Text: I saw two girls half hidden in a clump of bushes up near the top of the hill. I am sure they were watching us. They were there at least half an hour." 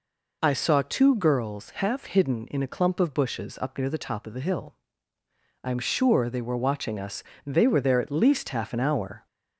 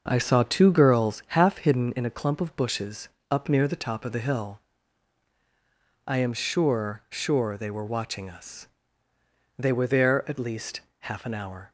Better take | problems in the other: first | starts louder than the rest; until 1.0 s; 6.5 dB // pauses between "bushes" and "up"; slight; at 3.0 s; 0.22 s long // says "sure" twice; at 7.0 s // pauses between "least" and "half"; slight; at 10.8 s; 0.18 s long

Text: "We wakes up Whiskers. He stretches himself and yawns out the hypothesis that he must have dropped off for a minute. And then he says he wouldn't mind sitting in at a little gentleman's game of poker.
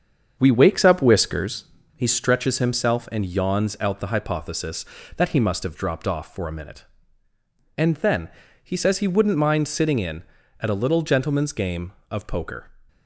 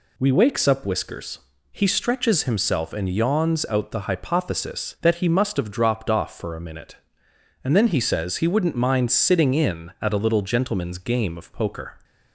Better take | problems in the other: second | starts louder than the rest; strong; until 1.6 s; 7 dB // pauses between "then" and "he"; slight; at 8.3 s; 0.32 s long

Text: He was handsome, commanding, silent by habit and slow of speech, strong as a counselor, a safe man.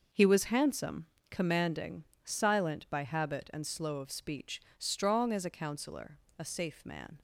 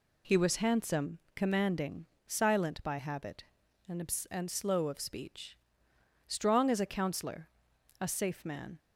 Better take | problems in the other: first | says "and" twice; at 4.2 s

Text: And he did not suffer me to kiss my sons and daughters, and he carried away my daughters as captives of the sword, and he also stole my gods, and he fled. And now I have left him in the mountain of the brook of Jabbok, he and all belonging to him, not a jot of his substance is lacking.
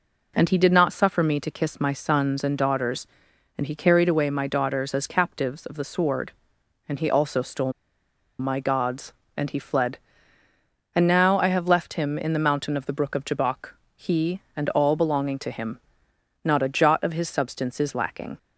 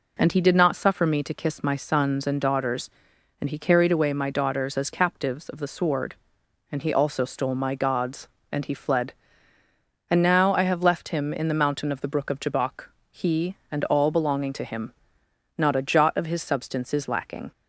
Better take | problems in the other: second | pauses between "stole" and "my"; noticeable; at 7.7 s; 0.67 s long

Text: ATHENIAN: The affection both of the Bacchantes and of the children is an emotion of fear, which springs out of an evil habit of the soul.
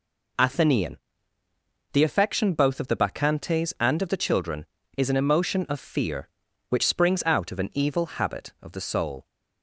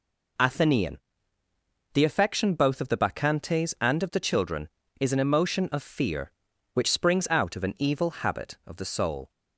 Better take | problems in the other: neither | none

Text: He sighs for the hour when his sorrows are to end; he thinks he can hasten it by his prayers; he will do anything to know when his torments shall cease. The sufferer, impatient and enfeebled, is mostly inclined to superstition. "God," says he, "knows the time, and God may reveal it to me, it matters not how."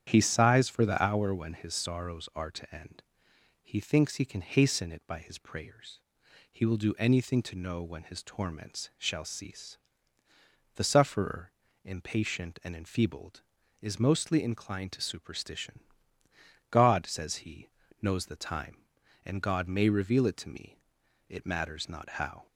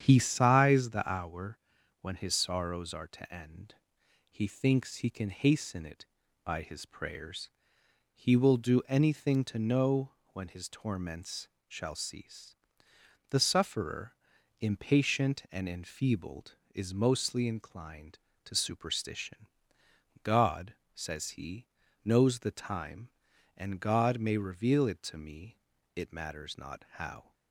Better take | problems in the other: first | starts louder than the rest; strong; until 1.0 s; 8.5 dB; strong in the first // skips "for"; at 0.8 s // pauses between "hour" and "when"; at 1.5 s; 0.42 s long // pauses between "know" and "when"; slight; at 10.0 s; 0.24 s long // pauses between "torments" and "shall"; slight; at 11.4 s; 0.18 s long

